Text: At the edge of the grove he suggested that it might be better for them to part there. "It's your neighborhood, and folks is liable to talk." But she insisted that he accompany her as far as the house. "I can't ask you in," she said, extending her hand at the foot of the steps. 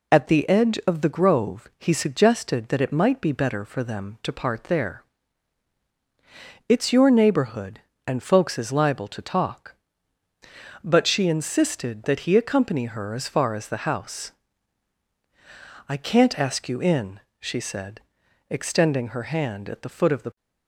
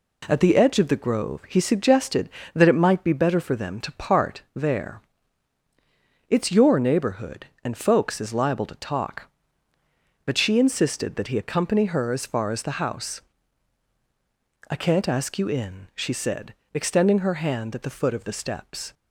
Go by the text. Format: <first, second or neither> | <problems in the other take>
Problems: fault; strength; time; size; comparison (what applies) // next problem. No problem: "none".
second | stops before "steps"; at 20.3 s